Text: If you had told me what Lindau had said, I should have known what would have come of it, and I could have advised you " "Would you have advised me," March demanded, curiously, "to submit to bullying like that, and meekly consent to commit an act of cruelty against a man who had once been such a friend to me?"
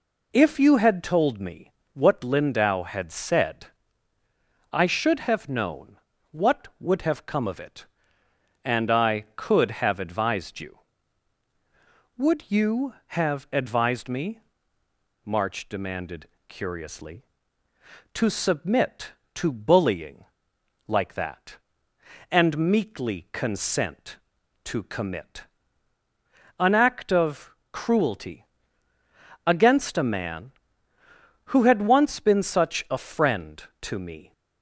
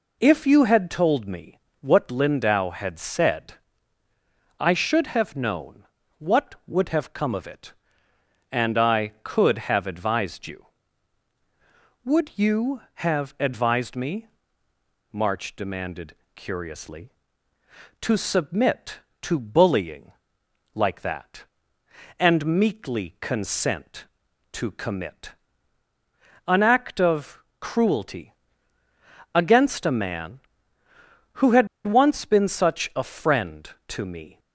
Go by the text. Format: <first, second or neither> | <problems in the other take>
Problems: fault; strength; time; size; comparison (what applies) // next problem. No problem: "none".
first | pauses between "me" and "what"; slight; at 1.5 s; 0.24 s long; slight in the first // pauses between "known" and "what"; slight; at 5.8 s; 0.36 s long; slight in the first // pauses between "bullying" and "like"; noticeable; at 20.1 s; 0.62 s long; noticeable in the first // pauses between "commit" and "an"; at 25.3 s; 1.1 s long; also in the first // pauses between "of" and "cruelty"; slight; at 27.4 s; 0.18 s long; slight in the first // pauses between "cruelty" and "against"; at 28.3 s; 1.0 s long; also in the first // pauses between "had" and "once"; slight; at 31.6 s; 0.19 s long